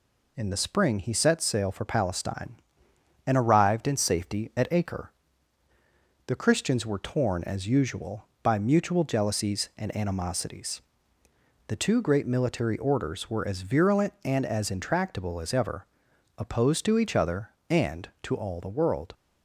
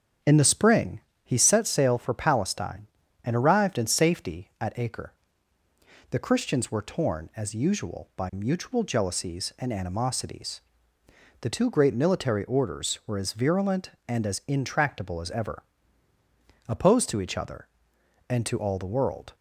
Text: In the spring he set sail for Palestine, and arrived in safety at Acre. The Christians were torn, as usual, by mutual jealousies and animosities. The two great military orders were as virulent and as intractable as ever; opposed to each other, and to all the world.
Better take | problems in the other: first | starts louder than the rest; strong; until 1.5 s; 7.5 dB // pauses between "spring" and "he"; slight; at 1.0 s; 0.24 s long

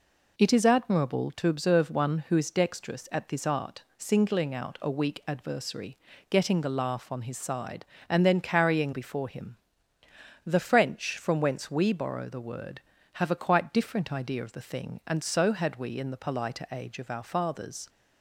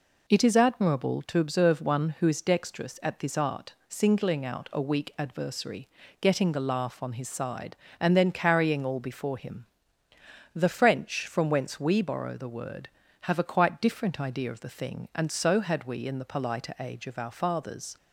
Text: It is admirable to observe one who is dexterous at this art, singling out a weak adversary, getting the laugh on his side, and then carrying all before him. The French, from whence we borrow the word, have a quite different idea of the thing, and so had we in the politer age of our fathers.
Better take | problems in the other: second | skips "all"; at 8.9 s

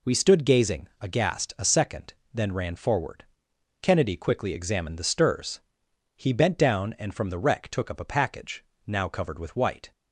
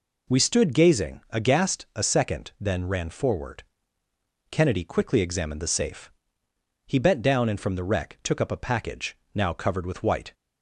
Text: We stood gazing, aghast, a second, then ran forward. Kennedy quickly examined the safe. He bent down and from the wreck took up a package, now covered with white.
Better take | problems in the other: second | says "stirs" for "safe"; at 5.0 s

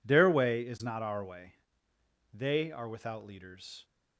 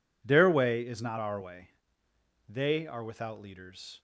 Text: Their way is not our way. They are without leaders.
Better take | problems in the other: neither | none

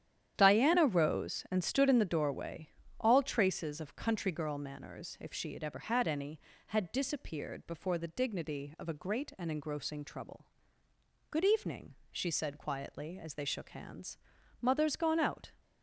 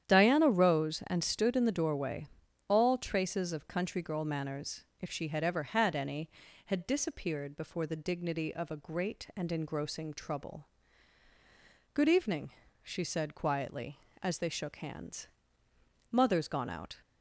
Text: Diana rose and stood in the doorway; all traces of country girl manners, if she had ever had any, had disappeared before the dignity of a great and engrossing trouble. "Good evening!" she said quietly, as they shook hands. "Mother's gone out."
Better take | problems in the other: neither | starts louder than the rest; strong; the same in both

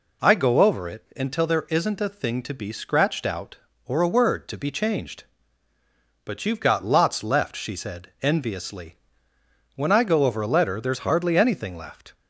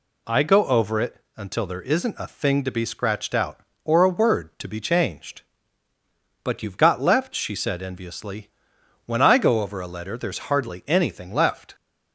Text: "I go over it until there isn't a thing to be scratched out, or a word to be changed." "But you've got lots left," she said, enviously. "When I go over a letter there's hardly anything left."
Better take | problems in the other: first | pauses between "it" and "until"; slight; at 1.2 s; 0.16 s long // skips "lots"; at 6.9 s

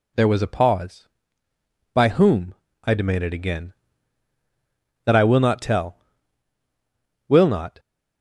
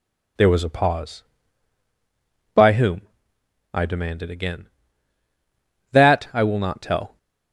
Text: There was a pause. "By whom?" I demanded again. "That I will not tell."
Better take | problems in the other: second | goes on to say "Will not"; from 7.2 s on; 0.50 s long

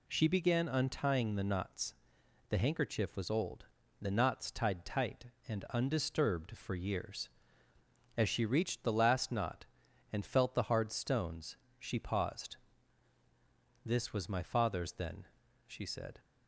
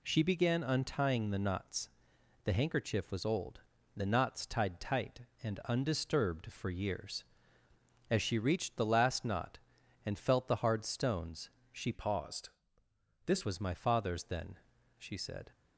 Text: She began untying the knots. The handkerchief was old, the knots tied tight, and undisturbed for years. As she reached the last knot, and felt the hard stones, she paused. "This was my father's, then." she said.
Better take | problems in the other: first | changes voice from "paused" to "This"; from 11.9 to 13.4 s; 1.5 s long

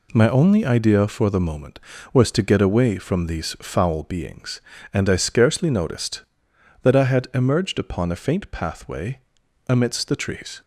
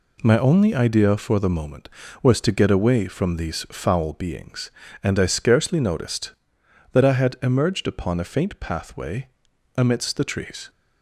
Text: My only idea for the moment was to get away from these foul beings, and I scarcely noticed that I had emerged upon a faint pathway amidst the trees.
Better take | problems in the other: neither | pauses between "pathway" and "amidst"; noticeable; the same in both

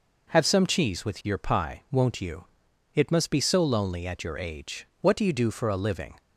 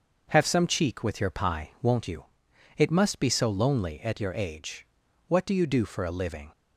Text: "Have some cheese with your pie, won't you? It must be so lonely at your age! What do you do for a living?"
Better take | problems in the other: first | starts louder than the rest; noticeable; until 1.3 s; 6 dB // says "cheek" for "cheese"; at 0.6 s

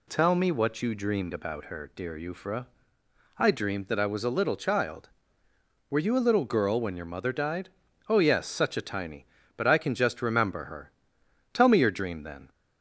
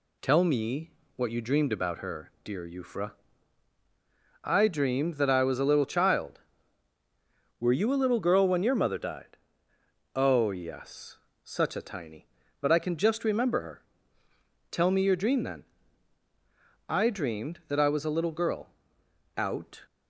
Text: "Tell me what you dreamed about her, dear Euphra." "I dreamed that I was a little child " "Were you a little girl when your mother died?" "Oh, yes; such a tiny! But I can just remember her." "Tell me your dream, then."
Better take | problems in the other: first | pauses between "me" and "what"; slight; at 0.9 s; 0.24 s long // goes on to say "I dreamed that I was a little girl out"; strong; from 16.8 s on; 2.9 s long

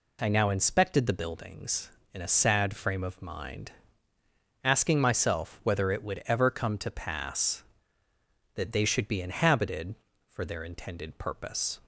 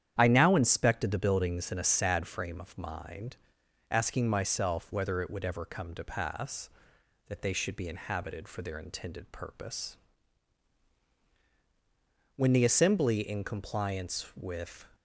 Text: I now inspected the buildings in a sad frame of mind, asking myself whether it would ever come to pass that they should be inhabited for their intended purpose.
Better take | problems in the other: first | starts louder than the rest; strong; until 1.1 s; 10 dB // goes on to say "When the Assembly in compliance with"; strong; from 12.3 s on; 2.5 s long

